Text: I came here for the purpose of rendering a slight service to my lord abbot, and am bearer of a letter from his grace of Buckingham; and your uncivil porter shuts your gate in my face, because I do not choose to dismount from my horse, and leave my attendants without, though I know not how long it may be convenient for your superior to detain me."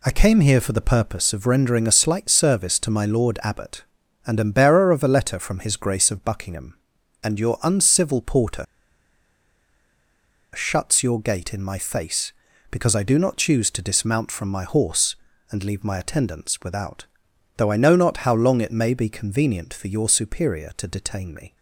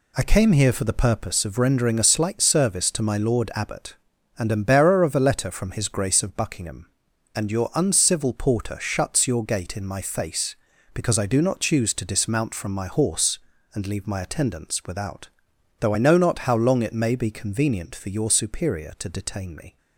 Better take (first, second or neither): second